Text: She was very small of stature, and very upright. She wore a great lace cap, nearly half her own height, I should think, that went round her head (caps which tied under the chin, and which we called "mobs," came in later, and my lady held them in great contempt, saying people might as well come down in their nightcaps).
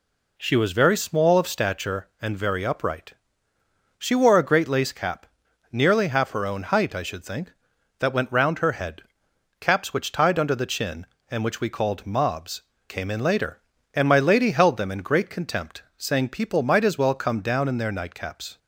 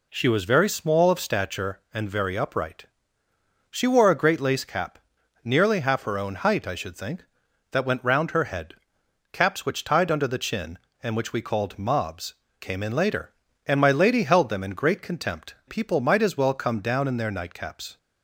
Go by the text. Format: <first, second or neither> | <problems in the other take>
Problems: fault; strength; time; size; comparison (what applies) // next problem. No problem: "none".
first | skips "saying"; at 15.6 s